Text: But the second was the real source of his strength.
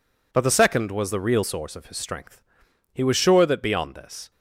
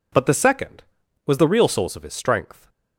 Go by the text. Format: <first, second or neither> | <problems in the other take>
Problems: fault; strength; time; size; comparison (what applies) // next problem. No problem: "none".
second | goes on to say "He was sure that beyond this"; from 2.9 s on; 1.3 s long